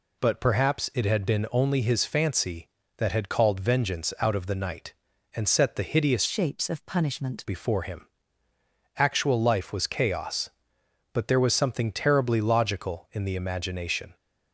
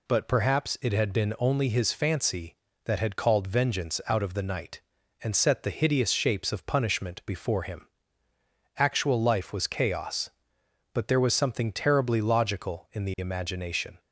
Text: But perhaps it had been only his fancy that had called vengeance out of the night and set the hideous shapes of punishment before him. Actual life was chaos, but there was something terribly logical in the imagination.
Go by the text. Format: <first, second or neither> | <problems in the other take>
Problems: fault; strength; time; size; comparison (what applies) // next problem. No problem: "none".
second | changes voice from "shapes" to "punishment"; from 6.2 to 7.4 s; 1.2 s long